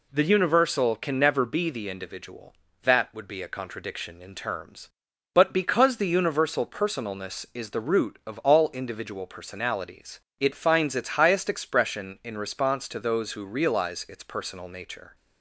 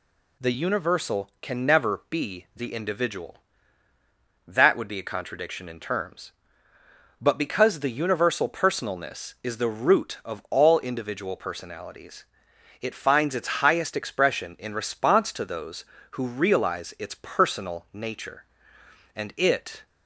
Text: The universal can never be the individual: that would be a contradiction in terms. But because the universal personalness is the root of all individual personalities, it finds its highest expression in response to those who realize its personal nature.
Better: first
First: none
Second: goes on to say "And it"; noticeable; from 19.1 s on; 0.70 s long

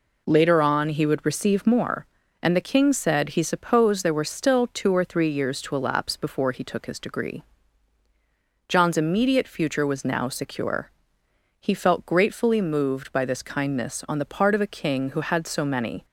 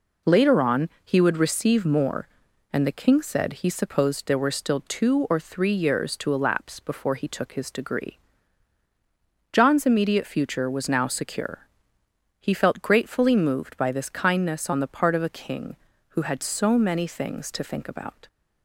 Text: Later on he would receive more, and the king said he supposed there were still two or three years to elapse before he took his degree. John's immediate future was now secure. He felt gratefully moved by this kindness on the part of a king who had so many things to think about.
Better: second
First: stops before "things to think about"; at 16.0 s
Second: none

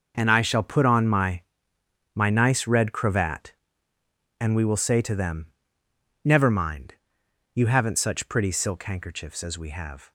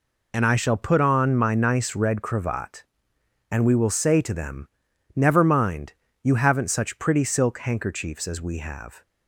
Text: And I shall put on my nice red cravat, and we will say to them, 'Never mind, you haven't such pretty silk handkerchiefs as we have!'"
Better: second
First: says "my" twice; at 2.1 s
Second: none

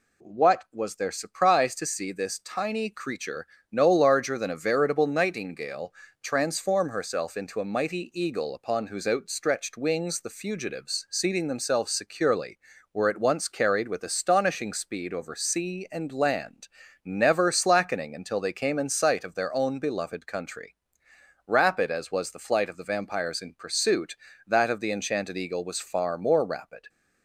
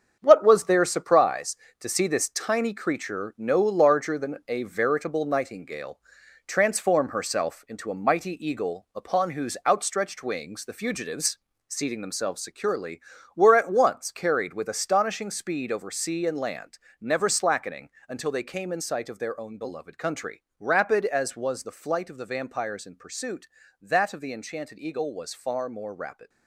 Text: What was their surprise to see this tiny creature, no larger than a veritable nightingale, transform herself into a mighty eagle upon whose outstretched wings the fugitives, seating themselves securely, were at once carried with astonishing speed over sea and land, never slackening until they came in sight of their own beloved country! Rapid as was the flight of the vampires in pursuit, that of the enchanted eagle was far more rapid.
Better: first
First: none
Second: gets quieter; strong; throughout; 8.5 dB // pauses between "slackening" and "until"; slight; at 17.8 s; 0.20 s long

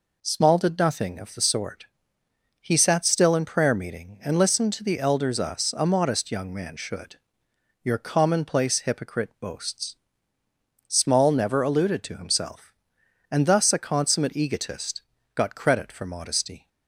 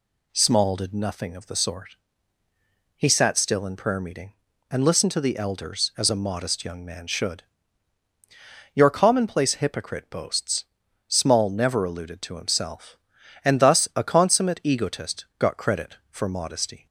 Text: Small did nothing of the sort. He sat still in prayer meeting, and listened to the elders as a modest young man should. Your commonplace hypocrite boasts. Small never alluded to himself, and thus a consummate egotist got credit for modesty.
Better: second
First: says "us" for "as"; at 5.4 s // pauses between "egotist" and "got"; slight; at 15.0 s; 0.32 s long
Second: none

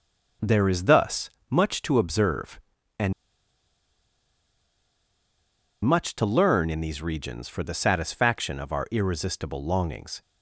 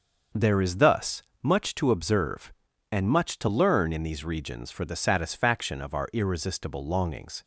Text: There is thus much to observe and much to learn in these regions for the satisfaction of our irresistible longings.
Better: second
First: starts louder than the rest; until 1.6 s; 6.5 dB // pauses between "thus" and "much"; slight; at 1.2 s; 0.20 s long // pauses between "and" and "much"; strong; at 3.1 s; 2.7 s long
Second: starts louder than the rest; until 1.5 s; 6 dB // pauses between "thus" and "much"; slight; at 1.2 s; 0.20 s long

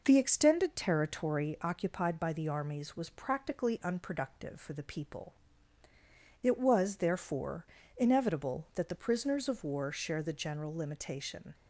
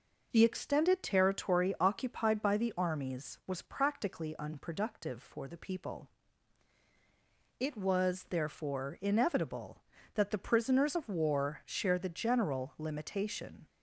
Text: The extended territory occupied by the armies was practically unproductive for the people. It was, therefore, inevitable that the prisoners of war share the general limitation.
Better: neither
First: none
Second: none

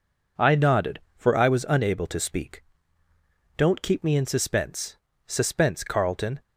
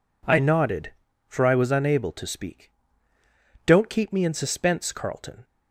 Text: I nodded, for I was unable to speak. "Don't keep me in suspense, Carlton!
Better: second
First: says "suspense" twice; at 5.2 s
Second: none

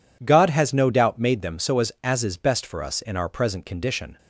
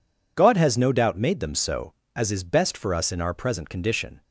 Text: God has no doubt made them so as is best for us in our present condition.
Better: second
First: says "as" twice; at 2.0 s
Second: none

